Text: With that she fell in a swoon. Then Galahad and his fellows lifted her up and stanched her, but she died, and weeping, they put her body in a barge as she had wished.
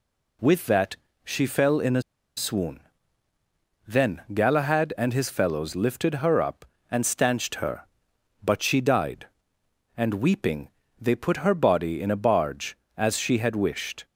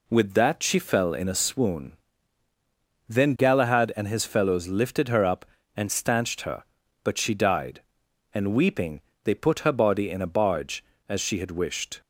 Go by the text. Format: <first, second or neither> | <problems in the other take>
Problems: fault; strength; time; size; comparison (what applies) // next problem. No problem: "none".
second | pauses between "that" and "she"; slight; at 0.9 s; 0.26 s long // pauses between "a" and "swoon"; slight; at 2.0 s; 0.35 s long